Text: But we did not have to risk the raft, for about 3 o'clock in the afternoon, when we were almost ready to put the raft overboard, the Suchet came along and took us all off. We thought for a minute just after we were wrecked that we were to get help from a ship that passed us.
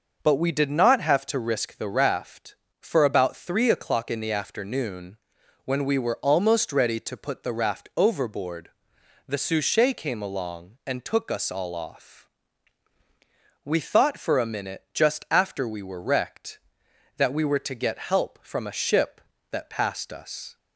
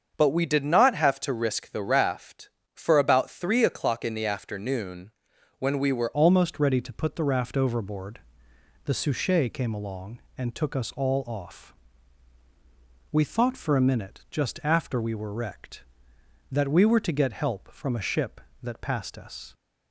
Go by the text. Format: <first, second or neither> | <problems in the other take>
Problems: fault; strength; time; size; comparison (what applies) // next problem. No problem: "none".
first | starts louder than the rest; until 1.1 s; 7 dB // changes voice at "almost"; from 6.1 s on; 13.4 s long